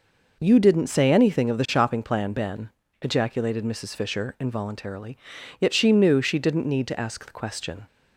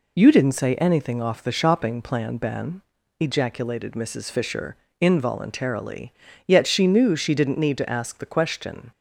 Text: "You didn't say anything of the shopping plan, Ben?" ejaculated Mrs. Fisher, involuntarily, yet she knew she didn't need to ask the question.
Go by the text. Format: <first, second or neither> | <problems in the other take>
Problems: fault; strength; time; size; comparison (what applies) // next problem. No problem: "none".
first | says "off" for "of"; at 1.2 s